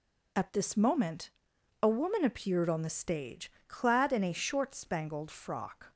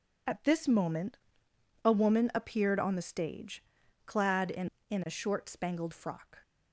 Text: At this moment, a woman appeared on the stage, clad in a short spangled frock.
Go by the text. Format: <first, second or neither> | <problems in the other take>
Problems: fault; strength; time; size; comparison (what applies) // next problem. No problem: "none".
first | says "in" twice; at 4.8 s